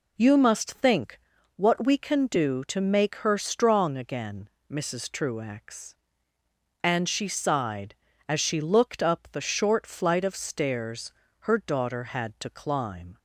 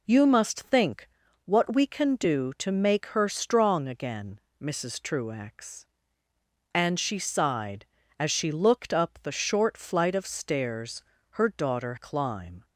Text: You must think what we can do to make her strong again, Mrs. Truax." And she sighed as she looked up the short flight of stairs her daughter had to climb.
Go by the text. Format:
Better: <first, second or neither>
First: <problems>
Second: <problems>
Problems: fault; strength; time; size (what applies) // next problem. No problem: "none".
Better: first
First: pauses between "think" and "what"; at 1.1 s; 0.38 s long // pauses between "stairs" and "her"; slight; at 11.1 s; 0.28 s long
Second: pauses between "think" and "what"; at 1.0 s; 0.38 s long // pauses between "stairs" and "her"; slight; at 11.0 s; 0.28 s long // skips "had to"; at 11.9 s